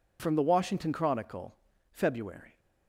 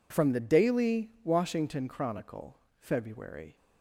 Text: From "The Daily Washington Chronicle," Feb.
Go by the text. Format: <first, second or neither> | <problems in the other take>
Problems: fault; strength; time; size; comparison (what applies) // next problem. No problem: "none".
second | skips "Daily"; at 0.4 s